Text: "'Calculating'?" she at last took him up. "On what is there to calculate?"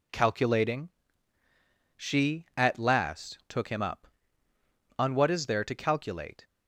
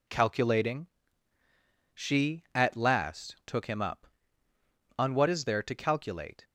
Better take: neither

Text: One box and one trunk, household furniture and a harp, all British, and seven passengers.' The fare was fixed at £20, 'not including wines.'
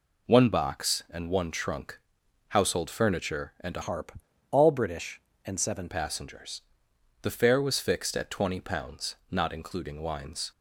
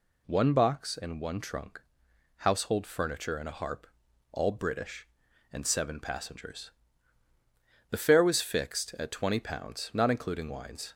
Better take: second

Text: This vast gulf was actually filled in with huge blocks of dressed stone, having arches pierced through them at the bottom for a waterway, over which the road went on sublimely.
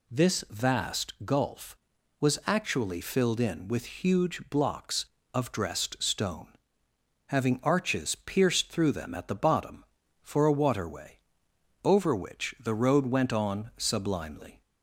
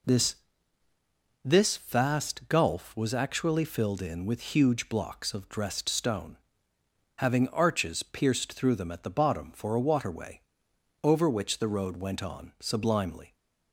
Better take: first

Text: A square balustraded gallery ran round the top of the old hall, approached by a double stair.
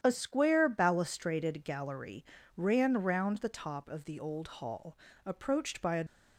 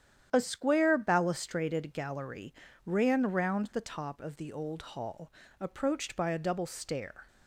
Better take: second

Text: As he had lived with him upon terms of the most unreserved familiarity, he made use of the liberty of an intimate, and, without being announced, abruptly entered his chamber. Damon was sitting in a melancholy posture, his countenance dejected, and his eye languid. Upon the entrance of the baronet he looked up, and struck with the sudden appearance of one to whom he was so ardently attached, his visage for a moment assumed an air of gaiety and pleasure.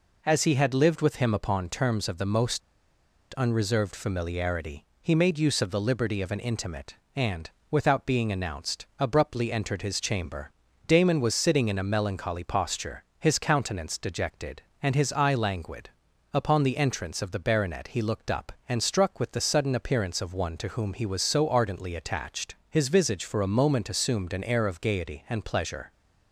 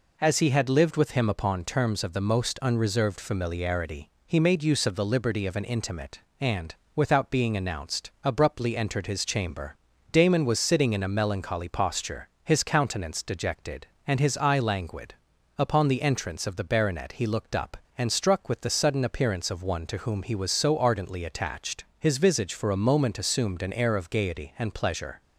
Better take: second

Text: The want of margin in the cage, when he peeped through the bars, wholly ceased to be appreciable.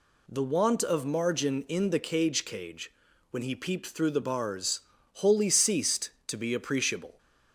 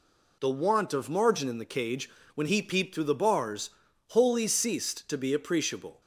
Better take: second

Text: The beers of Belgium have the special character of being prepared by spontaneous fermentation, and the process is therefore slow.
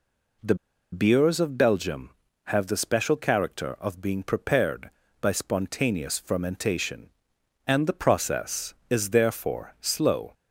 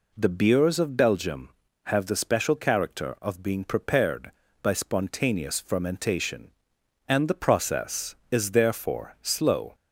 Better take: second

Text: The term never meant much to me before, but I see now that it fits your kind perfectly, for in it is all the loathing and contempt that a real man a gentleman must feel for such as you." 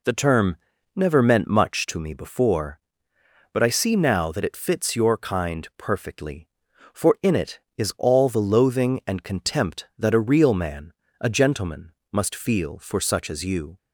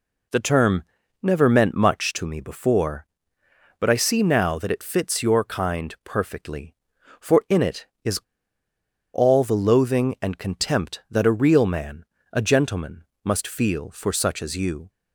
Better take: first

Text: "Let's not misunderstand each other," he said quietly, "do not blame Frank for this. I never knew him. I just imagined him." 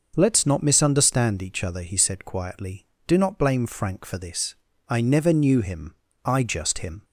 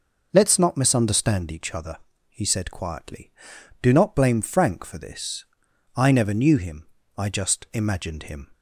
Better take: second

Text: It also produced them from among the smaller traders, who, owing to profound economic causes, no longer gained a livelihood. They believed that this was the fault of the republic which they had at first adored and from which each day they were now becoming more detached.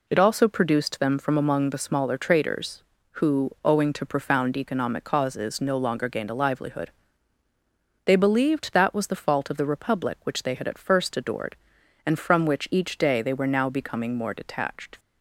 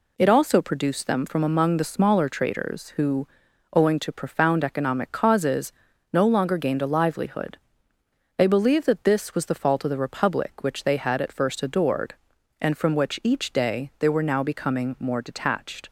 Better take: second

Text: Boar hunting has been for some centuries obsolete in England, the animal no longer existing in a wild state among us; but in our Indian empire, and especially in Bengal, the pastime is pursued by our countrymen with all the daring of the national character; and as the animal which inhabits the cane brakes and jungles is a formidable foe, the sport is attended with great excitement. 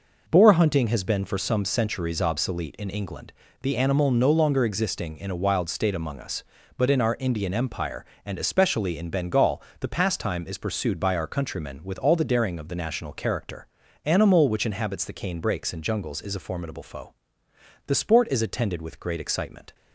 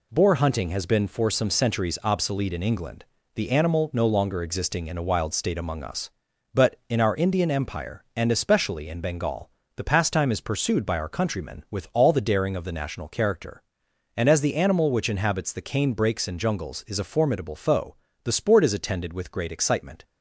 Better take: second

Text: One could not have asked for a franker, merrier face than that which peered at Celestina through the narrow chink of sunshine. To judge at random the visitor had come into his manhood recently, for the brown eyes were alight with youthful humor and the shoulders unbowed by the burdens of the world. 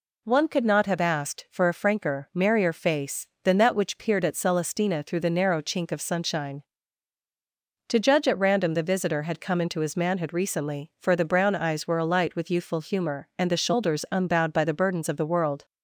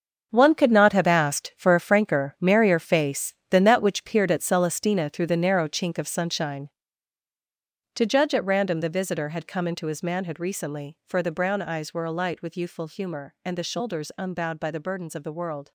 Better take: first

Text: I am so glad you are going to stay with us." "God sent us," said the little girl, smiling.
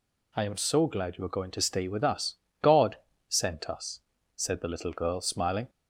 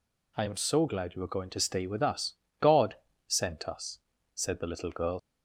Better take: first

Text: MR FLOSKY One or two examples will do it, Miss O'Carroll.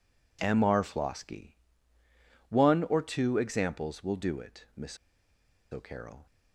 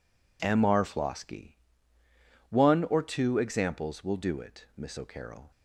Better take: second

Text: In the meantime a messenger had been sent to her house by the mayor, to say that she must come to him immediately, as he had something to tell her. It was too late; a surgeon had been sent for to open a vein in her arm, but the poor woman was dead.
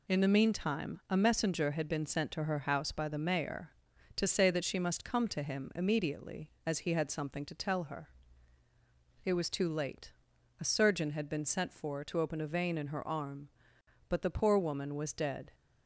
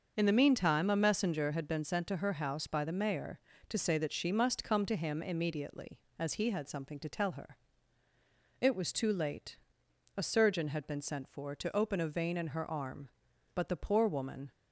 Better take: first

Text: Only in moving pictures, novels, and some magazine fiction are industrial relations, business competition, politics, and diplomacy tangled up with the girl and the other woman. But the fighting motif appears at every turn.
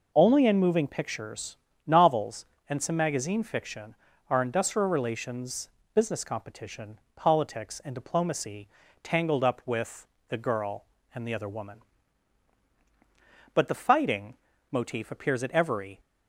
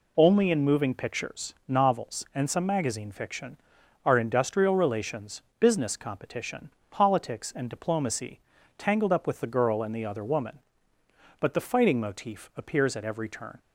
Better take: second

